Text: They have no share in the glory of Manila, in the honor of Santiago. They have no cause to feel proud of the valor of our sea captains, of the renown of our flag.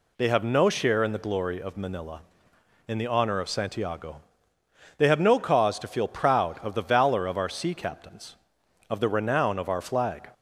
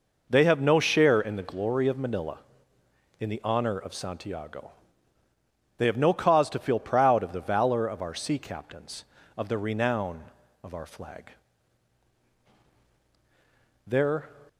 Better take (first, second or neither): first